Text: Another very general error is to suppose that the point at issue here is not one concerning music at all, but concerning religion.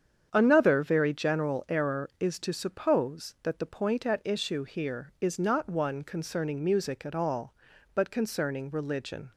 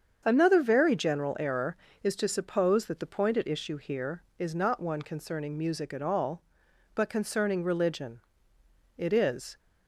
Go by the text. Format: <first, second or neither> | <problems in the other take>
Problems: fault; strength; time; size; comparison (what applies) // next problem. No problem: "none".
first | starts louder than the rest; strong; until 1.2 s; 7.5 dB; strong in the first // goes on to say "It is"; noticeable; from 8.9 s on; 0.62 s long